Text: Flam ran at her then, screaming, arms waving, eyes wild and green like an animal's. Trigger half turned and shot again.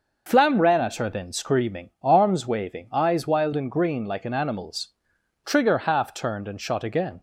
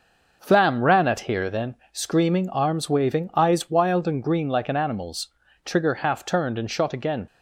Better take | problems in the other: first | says "here" for "her"; at 1.2 s

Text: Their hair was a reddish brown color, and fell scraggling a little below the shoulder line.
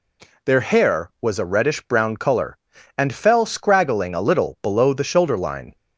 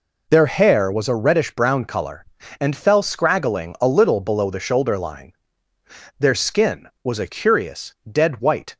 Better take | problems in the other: first | goes on to say "Their skin was a curious dead white"; strong; from 6.1 s on; 2.6 s long

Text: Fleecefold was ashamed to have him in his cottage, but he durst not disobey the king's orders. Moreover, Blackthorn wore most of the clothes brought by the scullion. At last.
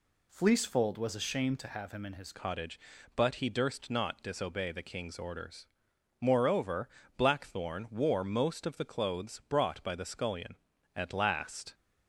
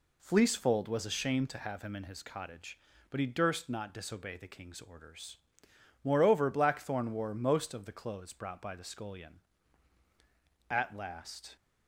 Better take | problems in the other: second | changes voice at "cottage"; from 2.3 s on; 9.4 s long

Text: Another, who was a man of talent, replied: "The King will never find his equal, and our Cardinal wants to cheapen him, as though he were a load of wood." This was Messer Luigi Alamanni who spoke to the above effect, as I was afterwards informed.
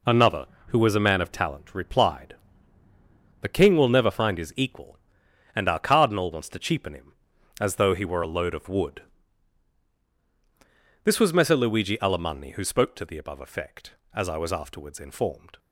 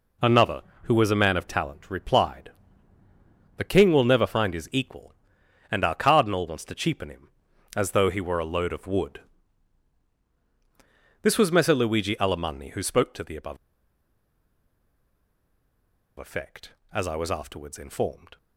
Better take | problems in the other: first | pauses between "above" and "effect"; strong; at 13.5 s; 2.6 s long

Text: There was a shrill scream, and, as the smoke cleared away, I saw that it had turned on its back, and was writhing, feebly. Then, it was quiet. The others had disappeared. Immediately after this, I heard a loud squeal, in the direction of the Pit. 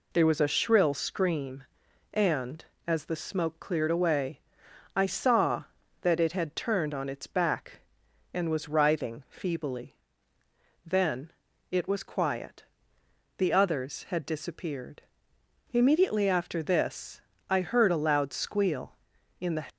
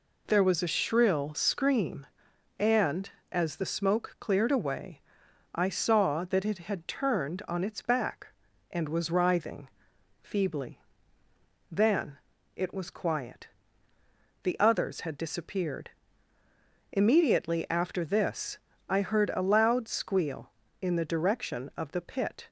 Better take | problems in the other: second | stops before "direction of the Pit"; at 19.7 s

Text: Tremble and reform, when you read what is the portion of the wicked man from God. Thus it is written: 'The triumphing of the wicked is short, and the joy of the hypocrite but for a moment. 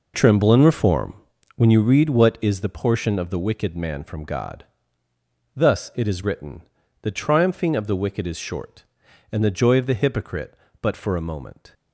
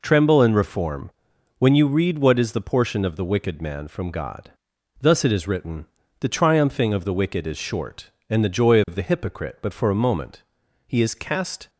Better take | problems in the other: first | goes on to say "He is cast"; noticeable; from 10.8 s on; 0.82 s long

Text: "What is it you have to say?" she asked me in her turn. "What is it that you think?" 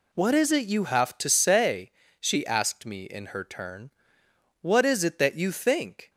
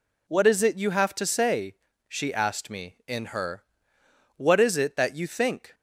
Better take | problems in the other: first | skips "turn"; at 4.0 s

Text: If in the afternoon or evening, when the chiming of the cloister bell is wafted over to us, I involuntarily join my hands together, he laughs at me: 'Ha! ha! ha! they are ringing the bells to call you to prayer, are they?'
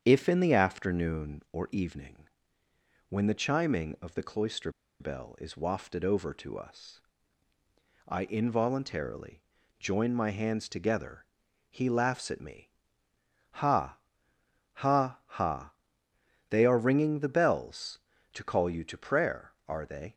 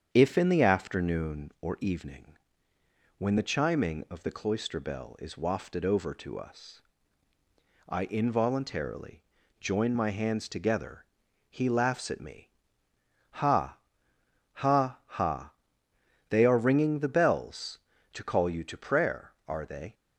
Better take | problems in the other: second | starts louder than the rest; strong; until 1.0 s; 8 dB; strong in the second // pauses between "cloister" and "bell"; slight; at 4.7 s; 0.28 s long // pauses between "involuntarily" and "join"; at 9.4 s; 0.38 s long; also in the second

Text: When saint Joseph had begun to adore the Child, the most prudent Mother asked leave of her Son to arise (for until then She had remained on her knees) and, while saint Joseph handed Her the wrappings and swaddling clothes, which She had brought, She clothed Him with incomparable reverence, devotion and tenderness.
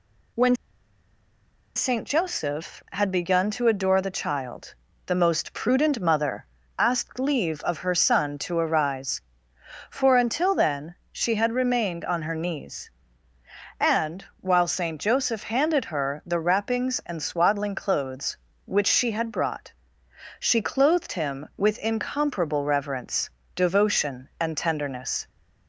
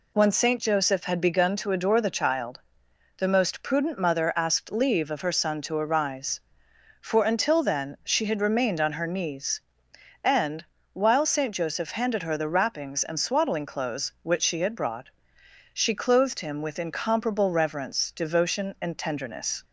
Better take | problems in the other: second | pauses between "When" and "saint"; at 0.5 s; 1.2 s long // pauses between "Mother" and "asked"; slight; at 6.4 s; 0.32 s long // pauses between "then" and "She"; slight; at 10.9 s; 0.16 s long

